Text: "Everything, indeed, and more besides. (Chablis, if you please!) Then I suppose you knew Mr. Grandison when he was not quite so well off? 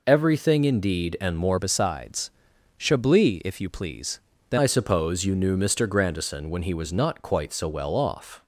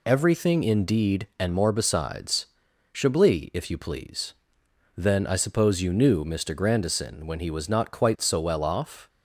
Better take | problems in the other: second | changes voice from "besides" to "Then"; from 1.5 to 4.5 s; 3.0 s long

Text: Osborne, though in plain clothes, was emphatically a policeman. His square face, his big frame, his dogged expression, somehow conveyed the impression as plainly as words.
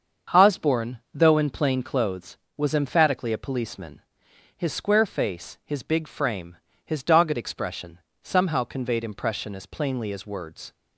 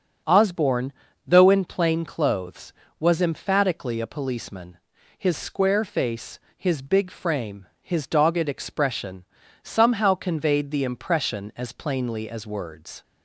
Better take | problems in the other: second | starts louder than the rest; until 1.4 s; 7 dB; also in the second // skips "the"; at 9.0 s

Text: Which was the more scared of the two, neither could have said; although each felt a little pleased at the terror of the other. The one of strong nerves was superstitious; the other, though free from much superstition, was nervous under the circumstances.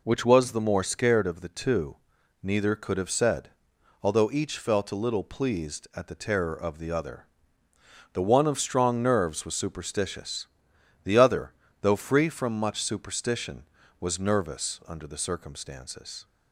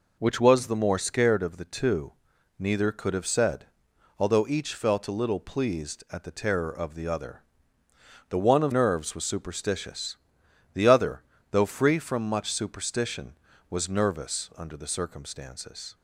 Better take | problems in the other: first | skips "strong"; at 8.7 s

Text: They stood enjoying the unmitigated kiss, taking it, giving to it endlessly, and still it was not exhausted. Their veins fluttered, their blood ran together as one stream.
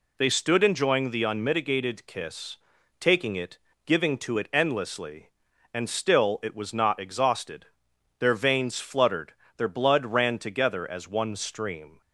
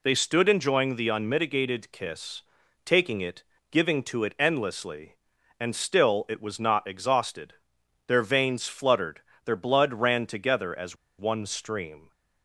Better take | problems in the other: first | pauses between "as" and "one"; slight; at 10.9 s; 0.24 s long

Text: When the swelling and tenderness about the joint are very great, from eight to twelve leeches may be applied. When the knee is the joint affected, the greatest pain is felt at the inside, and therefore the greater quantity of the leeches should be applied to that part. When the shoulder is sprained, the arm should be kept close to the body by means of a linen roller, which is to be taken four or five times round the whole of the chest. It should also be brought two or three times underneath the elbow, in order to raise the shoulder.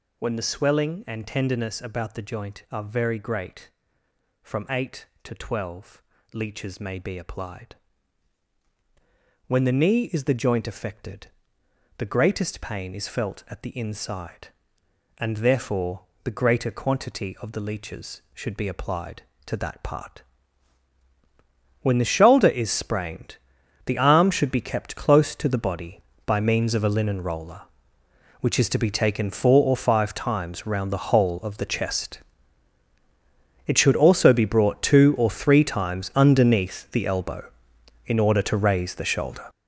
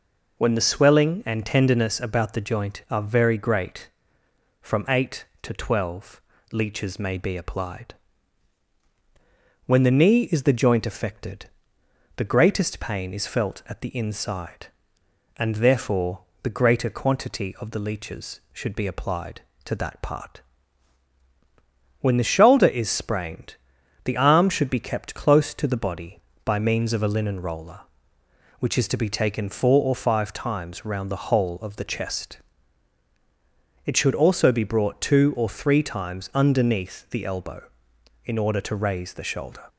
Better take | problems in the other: second | gets louder; strong; throughout; 11 dB // pauses between "twelve" and "leeches"; slight; at 6.0 s; 0.32 s long; slight in the second // pauses between "therefore" and "the"; slight; at 16.0 s; 0.24 s long; slight in the second

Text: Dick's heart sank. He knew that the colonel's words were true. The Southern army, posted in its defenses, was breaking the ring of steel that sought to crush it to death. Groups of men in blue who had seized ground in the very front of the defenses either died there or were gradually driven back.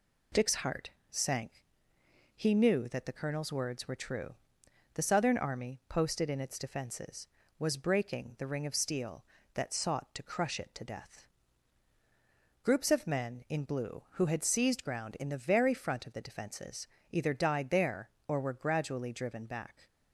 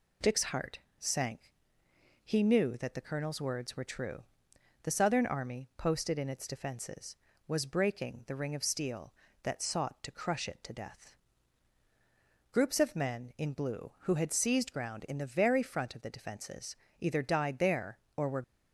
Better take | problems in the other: first | pauses between "heart" and "sank"; slight; at 0.7 s; 0.22 s long; slight in the first // pauses between "defenses" and "either"; slight; at 16.7 s; 0.24 s long; slight in the first // stops before "gradually driven back"; at 18.4 s

